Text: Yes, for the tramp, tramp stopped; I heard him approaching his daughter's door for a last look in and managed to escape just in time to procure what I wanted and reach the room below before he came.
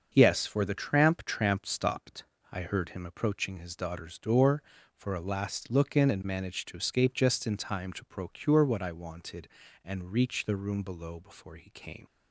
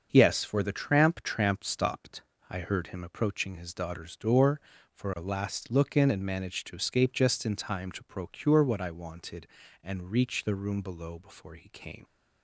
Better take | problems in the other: neither | starts louder than the rest; the same in both

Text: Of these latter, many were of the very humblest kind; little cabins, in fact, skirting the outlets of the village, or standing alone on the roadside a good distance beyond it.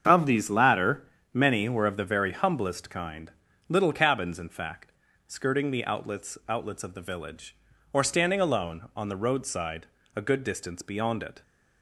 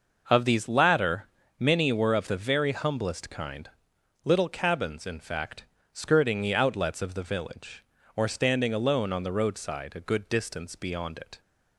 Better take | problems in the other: second | starts louder than the rest; strong; until 1.3 s; 7.5 dB // says "outlets" twice; at 6.4 s // pauses between "roadside" and "a"; slight; at 9.8 s; 0.26 s long

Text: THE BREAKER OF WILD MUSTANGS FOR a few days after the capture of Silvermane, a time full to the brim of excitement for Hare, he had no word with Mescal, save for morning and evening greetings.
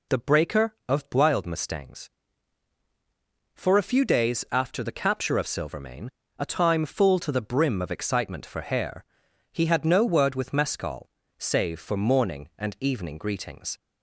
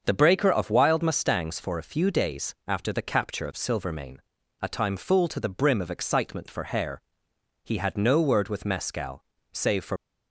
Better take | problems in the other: first | starts louder than the rest; until 1.0 s; 6.5 dB // stops before "morning and evening greetings"; at 9.9 s

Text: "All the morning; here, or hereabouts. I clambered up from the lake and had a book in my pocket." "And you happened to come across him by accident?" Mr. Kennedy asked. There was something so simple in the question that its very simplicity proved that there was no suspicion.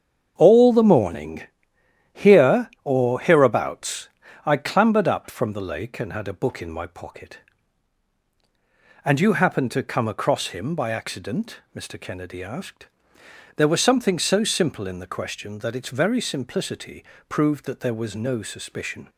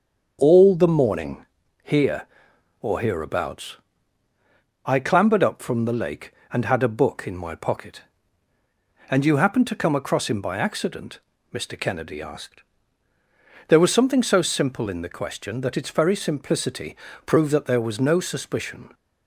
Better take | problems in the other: neither | starts louder than the rest; the same in both // pauses between "simplicity" and "proved"; slight; the same in both

